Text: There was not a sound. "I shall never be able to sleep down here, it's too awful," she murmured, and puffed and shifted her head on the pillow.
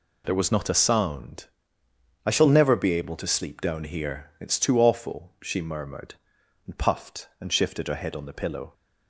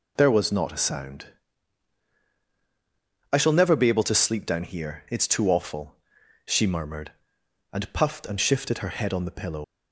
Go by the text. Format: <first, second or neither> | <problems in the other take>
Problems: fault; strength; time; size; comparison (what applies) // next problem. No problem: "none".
first | leaves "pillow" unfinished; at 9.6 s; 120 ms